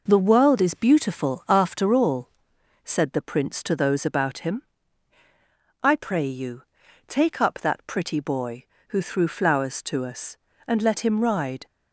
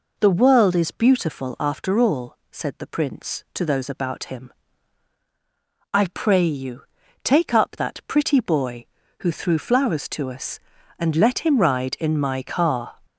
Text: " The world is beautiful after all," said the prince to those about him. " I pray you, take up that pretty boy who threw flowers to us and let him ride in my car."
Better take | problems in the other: second | stops before "in my car"; at 11.6 s

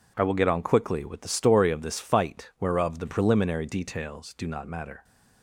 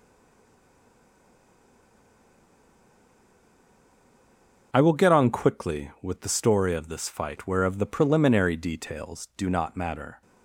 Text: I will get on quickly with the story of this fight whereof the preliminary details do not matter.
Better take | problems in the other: first | stays silent before the first word; strong; until 4.7 s; 4.7 s long // starts louder than the rest; until 5.7 s; 6.5 dB

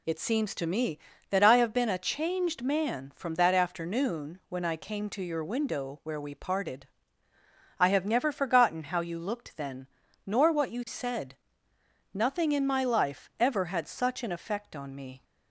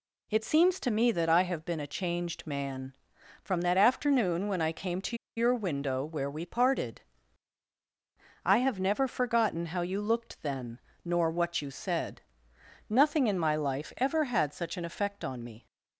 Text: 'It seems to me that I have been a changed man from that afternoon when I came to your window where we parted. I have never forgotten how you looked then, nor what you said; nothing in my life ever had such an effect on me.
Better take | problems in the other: first | pauses between "to" and "your"; slight; at 5.1 s; 0.20 s long

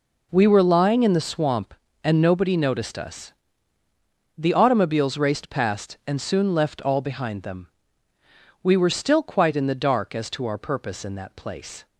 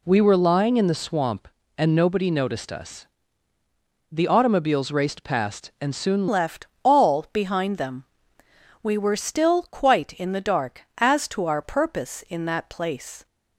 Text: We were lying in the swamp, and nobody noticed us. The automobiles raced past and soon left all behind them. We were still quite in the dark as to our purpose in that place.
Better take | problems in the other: first | changes voice at "left"; from 6.2 s on; 7.0 s long // pauses between "left" and "all"; slight; at 6.6 s; 0.16 s long

